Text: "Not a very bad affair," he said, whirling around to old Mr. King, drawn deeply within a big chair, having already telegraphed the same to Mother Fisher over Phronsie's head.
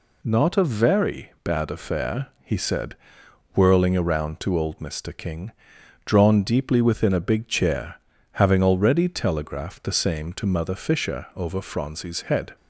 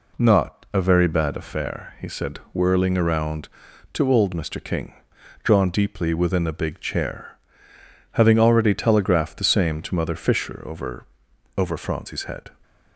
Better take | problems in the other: first | says "over" twice; at 11.5 s

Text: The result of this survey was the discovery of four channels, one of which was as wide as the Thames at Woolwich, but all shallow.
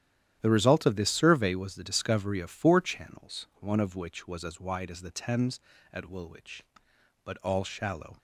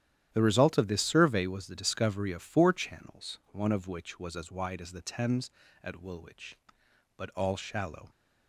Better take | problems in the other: neither | starts louder than the rest; strong; the same in both

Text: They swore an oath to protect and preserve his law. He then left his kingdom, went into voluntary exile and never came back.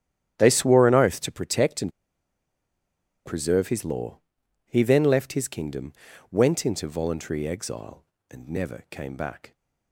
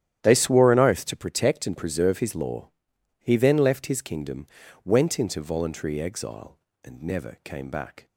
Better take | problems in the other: second | starts louder than the rest; strong; until 1.3 s; 11 dB; strong in the second // pauses between "and" and "preserve"; strong; at 1.9 s; 1.3 s long

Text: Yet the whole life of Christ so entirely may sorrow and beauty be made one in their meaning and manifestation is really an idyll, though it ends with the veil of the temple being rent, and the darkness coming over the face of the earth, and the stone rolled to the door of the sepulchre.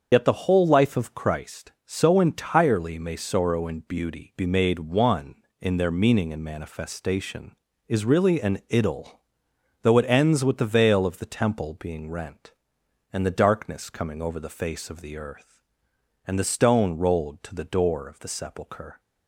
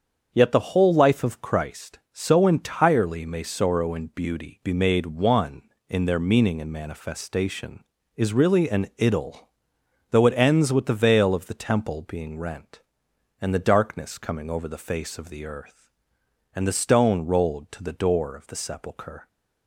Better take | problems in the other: second | loses the start of "Yet"; at 0.1 s; 50 ms // starts louder than the rest; until 1.1 s; 7 dB; also in the second

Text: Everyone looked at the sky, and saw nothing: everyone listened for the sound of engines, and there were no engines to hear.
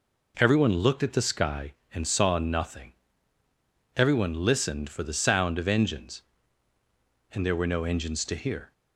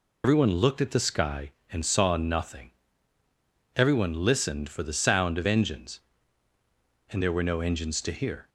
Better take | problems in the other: first | loses the start of "Everyone"; at 0.2 s; 115 ms

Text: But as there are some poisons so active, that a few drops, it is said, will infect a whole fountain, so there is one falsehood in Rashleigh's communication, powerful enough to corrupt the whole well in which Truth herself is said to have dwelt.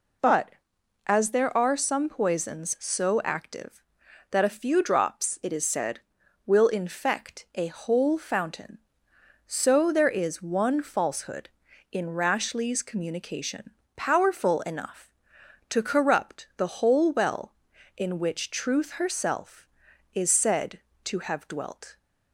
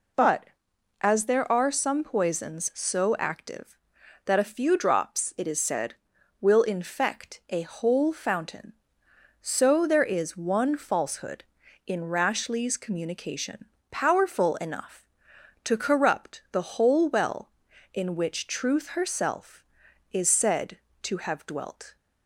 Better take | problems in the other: neither | none

